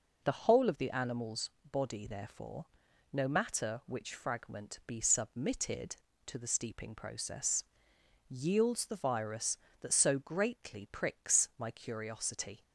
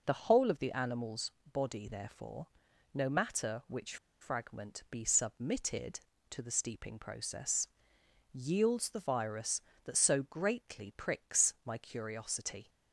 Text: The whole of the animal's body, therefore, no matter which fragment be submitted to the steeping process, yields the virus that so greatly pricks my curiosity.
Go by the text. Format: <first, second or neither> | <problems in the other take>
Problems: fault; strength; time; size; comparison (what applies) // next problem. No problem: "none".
first | pauses between "animal's" and "body"; slight; at 1.3 s; 0.20 s long; slight in the first // pauses between "which" and "fragment"; slight; at 3.9 s; 0.25 s long